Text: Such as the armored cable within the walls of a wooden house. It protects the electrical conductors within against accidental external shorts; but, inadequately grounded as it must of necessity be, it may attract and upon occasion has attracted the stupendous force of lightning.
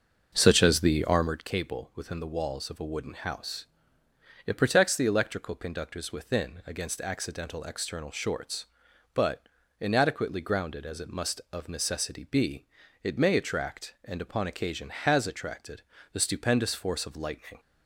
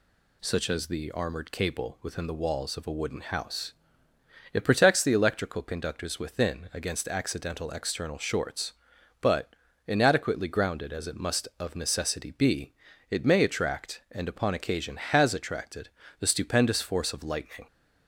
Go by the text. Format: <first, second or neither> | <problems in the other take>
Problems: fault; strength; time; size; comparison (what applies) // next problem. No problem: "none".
second | starts louder than the rest; until 1.5 s; 6 dB // pauses between "attracted" and "the"; slight; at 15.8 s; 0.30 s long; slight in the second